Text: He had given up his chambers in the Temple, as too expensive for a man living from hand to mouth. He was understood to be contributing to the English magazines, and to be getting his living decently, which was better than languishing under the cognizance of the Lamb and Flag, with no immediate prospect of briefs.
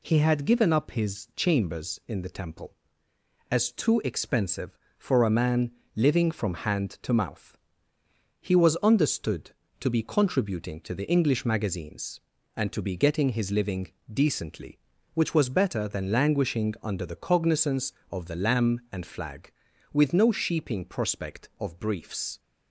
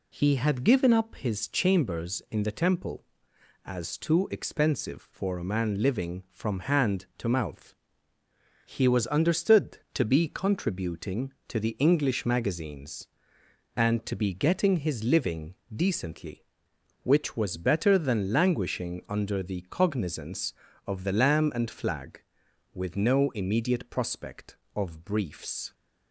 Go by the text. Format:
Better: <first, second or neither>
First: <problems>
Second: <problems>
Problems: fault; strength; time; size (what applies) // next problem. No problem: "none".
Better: second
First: pauses between "man" and "living"; slight; at 5.7 s; 0.24 s long // pauses between "living" and "decently"; slight; at 13.9 s; 0.22 s long // says "sheeping" for "immediate"; at 20.3 s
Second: pauses between "living" and "decently"; slight; at 15.5 s; 0.20 s long